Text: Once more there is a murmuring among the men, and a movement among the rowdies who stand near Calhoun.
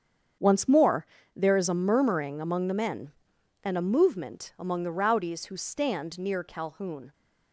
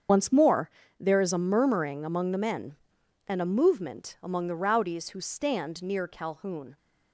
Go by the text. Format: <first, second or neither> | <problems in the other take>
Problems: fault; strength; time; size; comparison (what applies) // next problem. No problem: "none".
first | loses the start of "Once"; at 0.0 s; 55 ms // starts louder than the rest; strong; until 1.4 s; 7.5 dB; strong in the first // pauses between "more" and "there"; slight; at 0.6 s; 0.30 s long; slight in the first